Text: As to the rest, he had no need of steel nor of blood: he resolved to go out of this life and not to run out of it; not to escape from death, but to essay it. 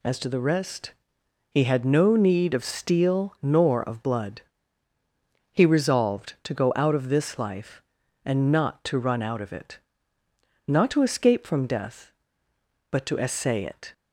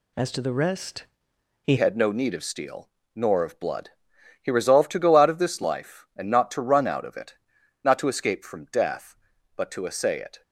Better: first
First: none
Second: changes voice at "had"; from 1.7 s on; 8.7 s long // pauses between "steel" and "nor"; slight; at 2.8 s; 0.26 s long

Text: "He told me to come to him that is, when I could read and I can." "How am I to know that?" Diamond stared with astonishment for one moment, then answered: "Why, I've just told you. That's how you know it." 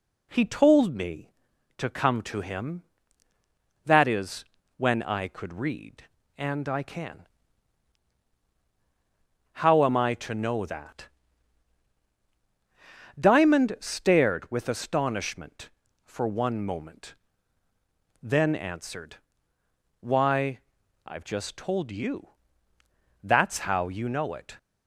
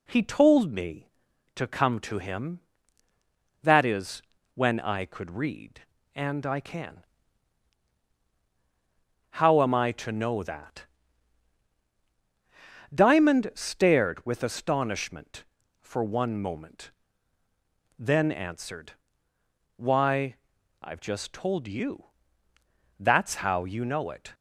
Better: neither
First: none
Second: none

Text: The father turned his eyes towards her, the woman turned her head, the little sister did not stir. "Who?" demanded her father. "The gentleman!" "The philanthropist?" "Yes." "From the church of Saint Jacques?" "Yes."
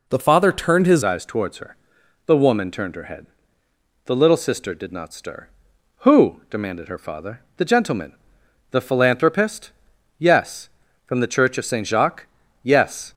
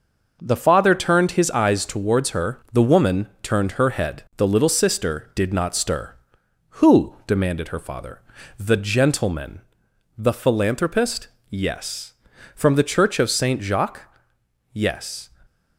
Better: second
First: changes voice at "eyes"; from 1.0 s on; 12.1 s long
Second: none

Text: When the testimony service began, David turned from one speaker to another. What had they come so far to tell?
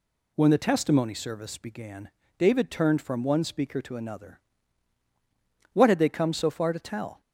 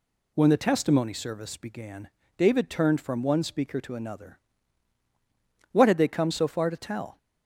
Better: neither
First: none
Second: none

